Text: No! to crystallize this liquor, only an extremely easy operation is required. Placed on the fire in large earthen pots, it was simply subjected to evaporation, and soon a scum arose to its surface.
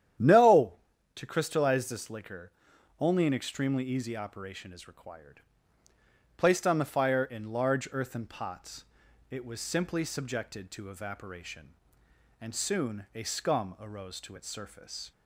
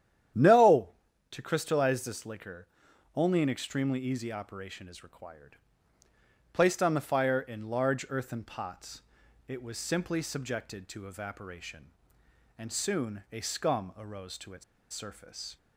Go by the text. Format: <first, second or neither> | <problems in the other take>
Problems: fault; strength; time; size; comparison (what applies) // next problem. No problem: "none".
first | starts louder than the rest; strong; until 1.7 s; 10 dB; strong in the first // pauses between "its" and "surface"; slight; at 14.6 s; 0.28 s long